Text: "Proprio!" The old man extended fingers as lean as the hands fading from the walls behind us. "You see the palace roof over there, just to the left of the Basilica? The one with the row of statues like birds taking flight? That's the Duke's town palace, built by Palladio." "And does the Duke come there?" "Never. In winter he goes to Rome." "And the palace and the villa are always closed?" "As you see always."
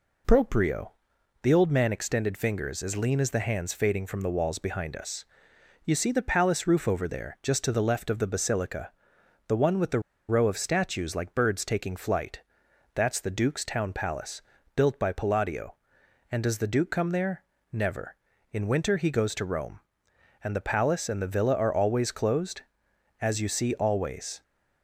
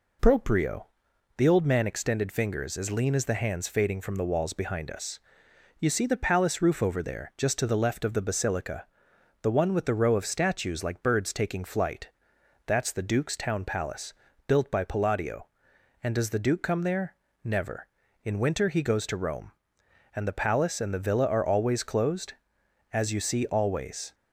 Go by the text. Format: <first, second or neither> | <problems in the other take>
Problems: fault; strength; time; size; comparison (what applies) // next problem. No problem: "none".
second | pauses between "the" and "row"; slight; at 9.9 s; 0.28 s long